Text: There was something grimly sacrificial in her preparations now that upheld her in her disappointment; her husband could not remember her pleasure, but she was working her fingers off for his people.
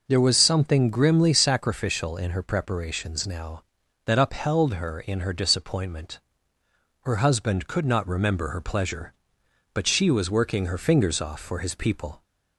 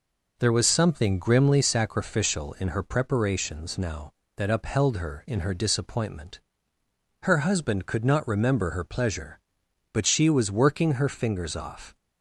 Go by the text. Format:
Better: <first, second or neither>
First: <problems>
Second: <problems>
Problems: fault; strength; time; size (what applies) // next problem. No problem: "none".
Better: first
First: none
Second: stops before "for his people"; at 11.9 s